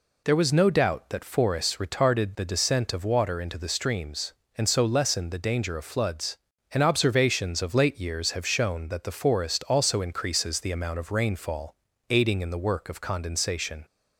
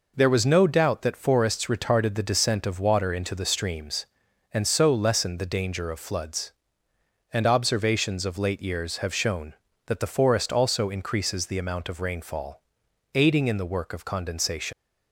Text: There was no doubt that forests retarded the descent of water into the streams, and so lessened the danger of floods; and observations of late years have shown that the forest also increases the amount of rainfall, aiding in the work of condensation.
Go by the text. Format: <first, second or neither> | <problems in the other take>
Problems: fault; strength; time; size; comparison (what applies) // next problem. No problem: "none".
first | leaves "condensation" unfinished; at 14.7 s; 100 ms